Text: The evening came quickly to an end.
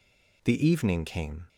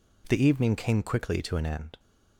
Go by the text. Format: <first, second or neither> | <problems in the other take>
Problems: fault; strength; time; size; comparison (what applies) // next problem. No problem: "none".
second | stops before "quickly to an end"; at 1.4 s